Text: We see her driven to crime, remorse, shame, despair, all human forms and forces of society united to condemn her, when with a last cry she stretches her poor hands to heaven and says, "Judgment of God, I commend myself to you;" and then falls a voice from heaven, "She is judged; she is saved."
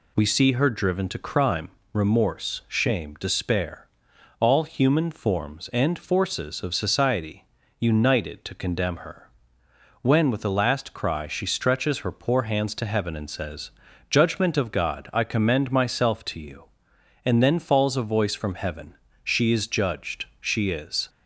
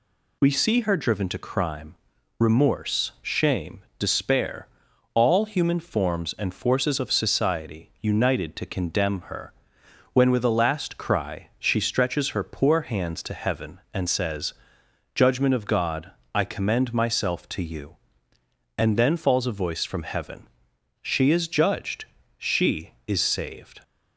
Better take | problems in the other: second | pauses between "society" and "united"; slight; at 7.4 s; 0.34 s long // stops before "saved"; at 21.0 s

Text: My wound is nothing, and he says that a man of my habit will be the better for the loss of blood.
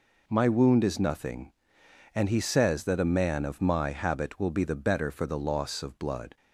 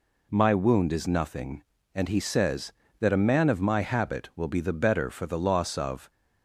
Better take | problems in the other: first | stops before "blood"; at 6.0 s

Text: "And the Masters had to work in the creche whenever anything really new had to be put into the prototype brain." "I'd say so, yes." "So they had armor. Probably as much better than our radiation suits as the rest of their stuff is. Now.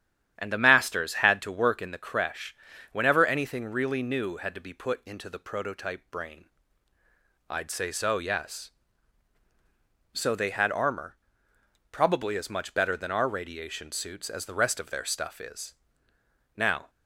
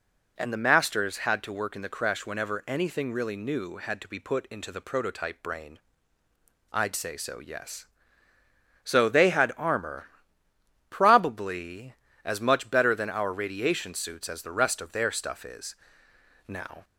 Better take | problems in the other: second | starts louder than the rest; strong; until 2.0 s; 10.5 dB // pauses between "creche" and "whenever"; slight; at 2.5 s; 0.36 s long

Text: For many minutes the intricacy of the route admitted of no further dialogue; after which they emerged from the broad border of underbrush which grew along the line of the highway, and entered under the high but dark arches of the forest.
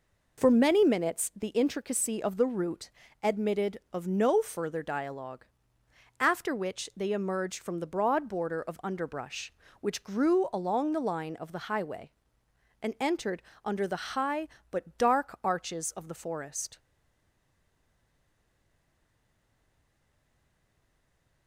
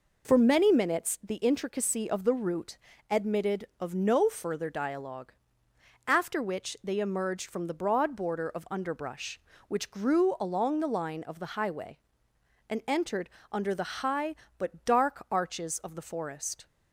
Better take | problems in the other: second | pauses between "route" and "admitted"; slight; at 2.9 s; 0.30 s long; slight in the second // pauses between "entered" and "under"; slight; at 13.4 s; 0.22 s long; slight in the second // stays silent after the last word; strong; from 16.7 s on; 4.7 s long

